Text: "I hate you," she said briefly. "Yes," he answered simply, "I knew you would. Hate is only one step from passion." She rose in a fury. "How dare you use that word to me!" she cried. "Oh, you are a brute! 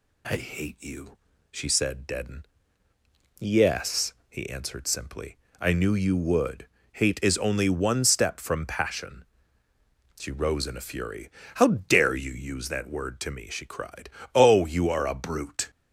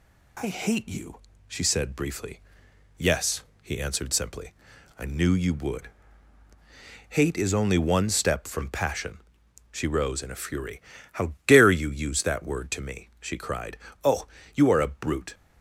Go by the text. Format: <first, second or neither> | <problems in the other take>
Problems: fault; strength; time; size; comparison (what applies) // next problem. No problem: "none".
second | says "deaden" for "briefly"; at 2.0 s